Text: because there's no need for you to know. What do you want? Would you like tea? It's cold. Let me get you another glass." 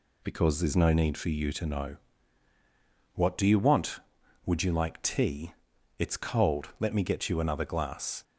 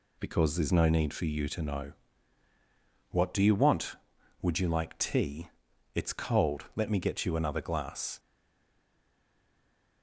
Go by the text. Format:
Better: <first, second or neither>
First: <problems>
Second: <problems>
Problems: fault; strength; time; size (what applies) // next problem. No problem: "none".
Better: first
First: none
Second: stays silent after the last word; noticeable; from 8.1 s on; 1.9 s long